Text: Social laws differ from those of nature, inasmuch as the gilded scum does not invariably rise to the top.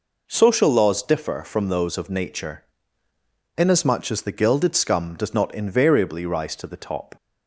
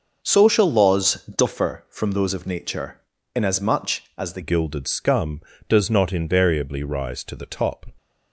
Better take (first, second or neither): first